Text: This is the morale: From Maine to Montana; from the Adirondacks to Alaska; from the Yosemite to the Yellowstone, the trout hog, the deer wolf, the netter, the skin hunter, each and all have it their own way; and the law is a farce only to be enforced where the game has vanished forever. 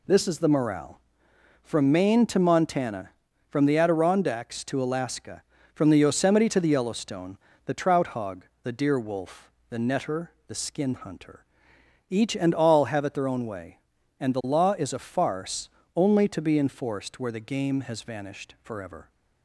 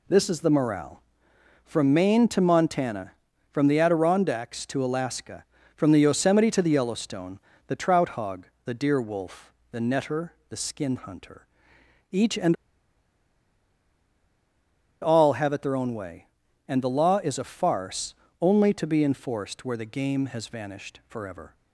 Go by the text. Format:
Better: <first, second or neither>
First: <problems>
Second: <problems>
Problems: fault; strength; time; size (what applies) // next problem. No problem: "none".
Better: first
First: pauses between "farce" and "only"; slight; at 15.7 s; 0.24 s long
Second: pauses between "and" and "all"; strong; at 12.5 s; 2.4 s long // pauses between "farce" and "only"; slight; at 18.1 s; 0.24 s long